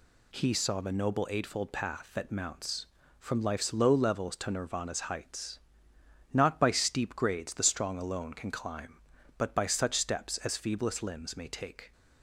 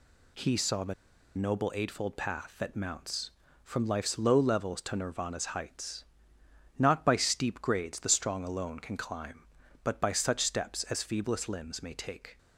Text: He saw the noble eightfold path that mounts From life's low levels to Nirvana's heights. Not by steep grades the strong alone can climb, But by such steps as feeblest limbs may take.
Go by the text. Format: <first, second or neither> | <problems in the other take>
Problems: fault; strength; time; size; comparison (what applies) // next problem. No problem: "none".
first | pauses between "the" and "noble"; at 0.9 s; 0.43 s long